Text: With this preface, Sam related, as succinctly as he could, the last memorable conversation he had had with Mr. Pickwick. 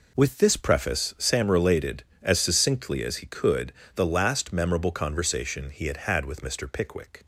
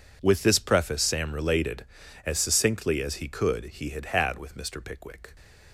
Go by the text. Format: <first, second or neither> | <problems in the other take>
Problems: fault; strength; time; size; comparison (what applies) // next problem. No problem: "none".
first | skips "the last memorable conversation"; at 3.6 s